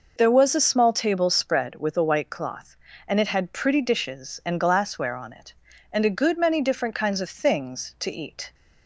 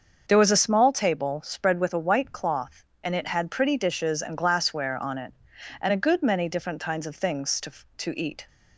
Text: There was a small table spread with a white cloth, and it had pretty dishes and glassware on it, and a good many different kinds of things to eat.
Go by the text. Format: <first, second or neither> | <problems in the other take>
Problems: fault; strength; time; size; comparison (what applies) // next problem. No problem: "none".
first | starts louder than the rest; until 1.2 s; 6.5 dB // says "to" twice; at 7.9 s